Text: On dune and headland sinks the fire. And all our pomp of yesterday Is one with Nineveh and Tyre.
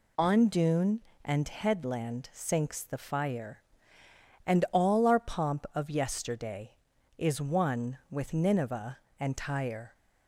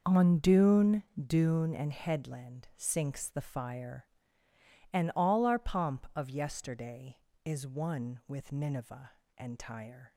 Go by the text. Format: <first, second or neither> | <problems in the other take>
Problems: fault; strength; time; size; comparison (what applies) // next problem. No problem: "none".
first | says "dune" twice; at 1.1 s